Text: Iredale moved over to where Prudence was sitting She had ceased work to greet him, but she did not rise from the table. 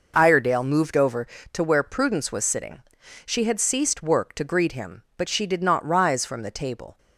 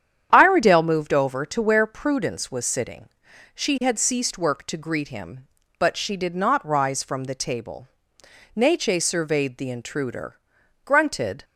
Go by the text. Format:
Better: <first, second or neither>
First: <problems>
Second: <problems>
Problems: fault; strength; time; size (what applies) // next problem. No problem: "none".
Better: first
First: pauses between "sitting" and "She"; at 2.8 s; 0.44 s long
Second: starts louder than the rest; strong; until 1.3 s; 9 dB // pauses between "sitting" and "She"; at 3.0 s; 0.44 s long // goes on to say "Neche surveyed the intruder grunted"; strong; from 8.5 s on; 2.9 s long